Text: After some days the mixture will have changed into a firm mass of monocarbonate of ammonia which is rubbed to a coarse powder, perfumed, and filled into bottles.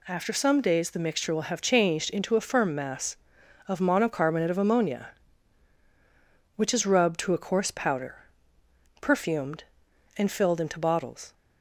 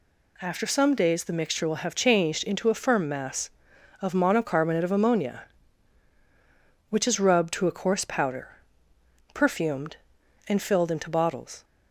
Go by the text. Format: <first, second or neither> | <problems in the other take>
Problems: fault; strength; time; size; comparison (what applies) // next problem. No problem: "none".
neither | none